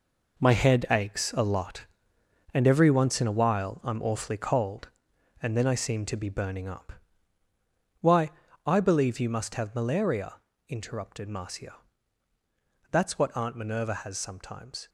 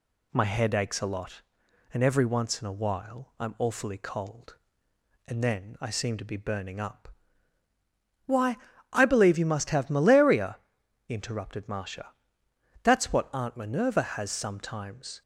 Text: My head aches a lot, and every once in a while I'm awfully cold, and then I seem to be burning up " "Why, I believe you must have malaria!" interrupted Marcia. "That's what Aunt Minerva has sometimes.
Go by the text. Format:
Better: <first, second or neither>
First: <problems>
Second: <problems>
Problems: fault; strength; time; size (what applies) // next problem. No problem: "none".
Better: second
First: gets quieter; strong; throughout; 9.5 dB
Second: none